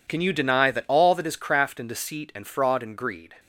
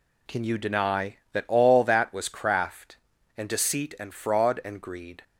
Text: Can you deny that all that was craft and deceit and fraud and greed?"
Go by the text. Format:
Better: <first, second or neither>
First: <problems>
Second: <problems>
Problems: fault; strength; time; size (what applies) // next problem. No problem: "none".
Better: second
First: says "is" for "was"; at 1.2 s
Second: none